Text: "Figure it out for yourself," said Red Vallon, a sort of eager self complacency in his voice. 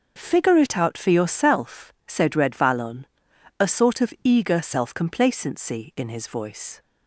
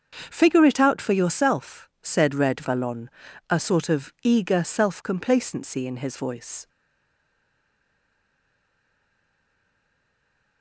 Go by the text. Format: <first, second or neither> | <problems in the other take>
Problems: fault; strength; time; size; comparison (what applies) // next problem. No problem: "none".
first | starts louder than the rest; until 1.3 s; 7 dB // stays silent after the last word; strong; from 6.6 s on; 4.0 s long